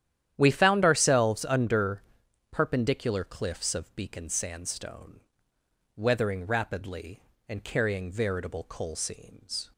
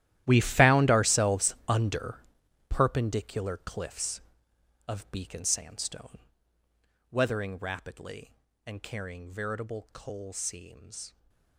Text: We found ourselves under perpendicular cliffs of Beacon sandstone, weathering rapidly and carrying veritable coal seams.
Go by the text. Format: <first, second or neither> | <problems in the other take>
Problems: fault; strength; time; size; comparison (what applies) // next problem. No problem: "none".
first | gets quieter; strong; throughout; 17.5 dB // starts louder than the rest; strong; until 1.2 s; 13 dB; strong in the first // pauses between "under" and "perpendicular"; noticeable; at 2.1 s; 0.50 s long; noticeable in the first